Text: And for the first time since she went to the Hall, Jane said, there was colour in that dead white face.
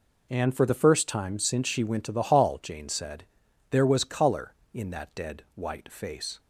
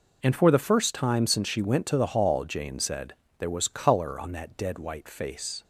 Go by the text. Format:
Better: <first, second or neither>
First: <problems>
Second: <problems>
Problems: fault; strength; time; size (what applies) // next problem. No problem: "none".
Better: first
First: none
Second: says "on" for "in"; at 4.1 s